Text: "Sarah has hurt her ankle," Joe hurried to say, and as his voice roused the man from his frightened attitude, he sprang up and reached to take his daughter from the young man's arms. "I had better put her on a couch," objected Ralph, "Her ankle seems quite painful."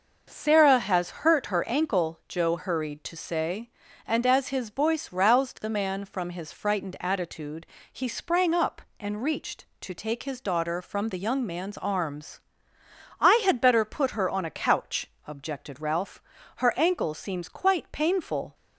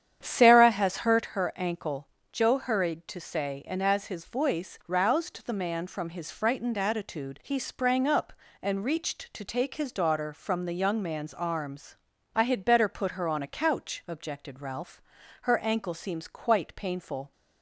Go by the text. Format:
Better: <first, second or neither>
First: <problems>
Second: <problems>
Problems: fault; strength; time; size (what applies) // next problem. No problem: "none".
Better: first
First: none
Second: starts louder than the rest; strong; until 1.3 s; 9 dB